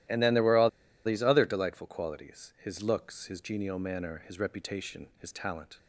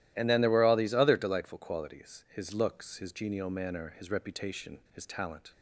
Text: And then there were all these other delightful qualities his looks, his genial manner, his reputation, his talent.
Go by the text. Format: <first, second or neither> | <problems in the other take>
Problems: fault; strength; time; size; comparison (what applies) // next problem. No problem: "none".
second | starts louder than the rest; strong; until 1.4 s; 13.5 dB; strong in the second // pauses between "all" and "these"; slight; at 0.6 s; 0.35 s long